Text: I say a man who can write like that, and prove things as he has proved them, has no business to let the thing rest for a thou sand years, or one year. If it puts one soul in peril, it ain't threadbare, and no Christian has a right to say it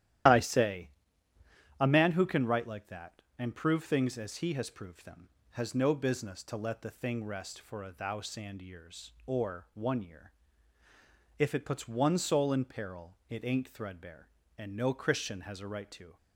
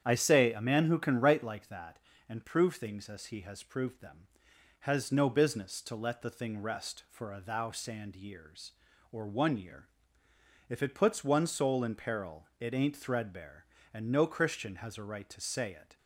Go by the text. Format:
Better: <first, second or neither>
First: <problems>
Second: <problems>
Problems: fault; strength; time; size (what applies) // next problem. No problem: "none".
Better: second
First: starts louder than the rest; strong; until 2.1 s; 12 dB // pauses between "say" and "a"; noticeable; at 0.8 s; 0.90 s long // stops before "say it"; at 16.1 s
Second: starts louder than the rest; strong; until 1.0 s; 9 dB